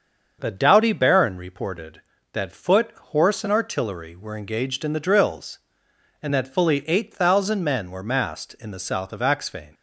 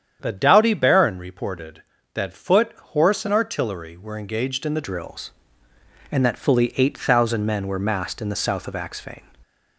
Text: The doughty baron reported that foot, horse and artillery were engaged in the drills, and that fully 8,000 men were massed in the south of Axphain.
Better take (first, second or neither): first